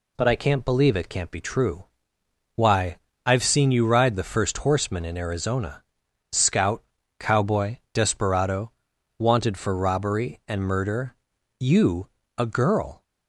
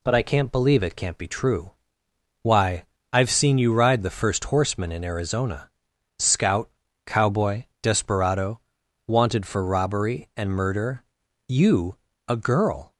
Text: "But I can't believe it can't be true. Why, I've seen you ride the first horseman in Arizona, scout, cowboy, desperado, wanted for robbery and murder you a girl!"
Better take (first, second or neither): neither